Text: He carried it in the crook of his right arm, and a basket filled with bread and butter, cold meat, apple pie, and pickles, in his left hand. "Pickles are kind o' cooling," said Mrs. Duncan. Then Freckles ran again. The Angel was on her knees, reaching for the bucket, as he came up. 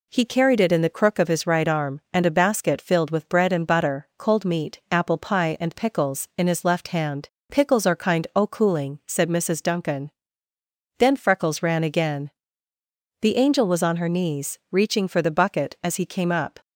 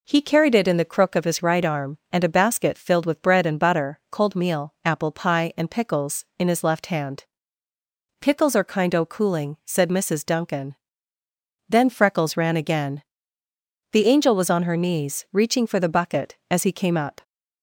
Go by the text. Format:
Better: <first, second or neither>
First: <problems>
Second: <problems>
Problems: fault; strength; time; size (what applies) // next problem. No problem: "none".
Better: first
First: none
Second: says "meal" for "meat"; at 4.3 s